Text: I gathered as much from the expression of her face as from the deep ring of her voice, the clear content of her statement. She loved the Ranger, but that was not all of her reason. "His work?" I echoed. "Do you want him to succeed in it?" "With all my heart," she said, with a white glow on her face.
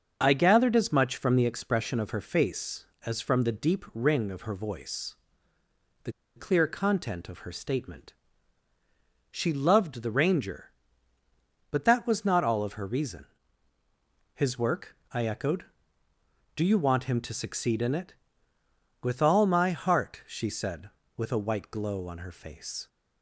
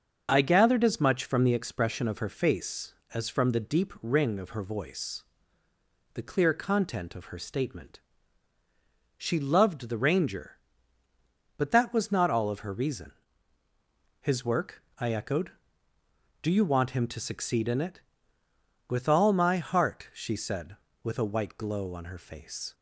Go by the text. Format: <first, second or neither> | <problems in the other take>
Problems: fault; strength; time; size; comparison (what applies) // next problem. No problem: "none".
second | starts louder than the rest; until 1.2 s; 6.5 dB; also in the second // pauses between "the" and "clear"; slight; at 6.1 s; 0.24 s long